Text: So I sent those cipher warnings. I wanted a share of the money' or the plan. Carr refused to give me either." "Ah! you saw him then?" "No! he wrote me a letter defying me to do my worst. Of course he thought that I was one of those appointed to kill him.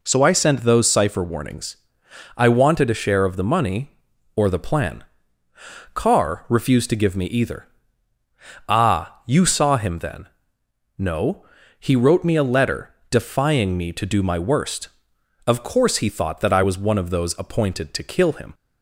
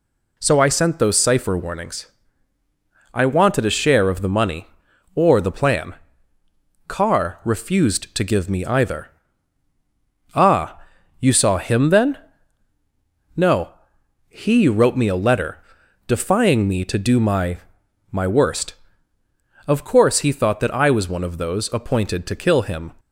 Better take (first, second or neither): first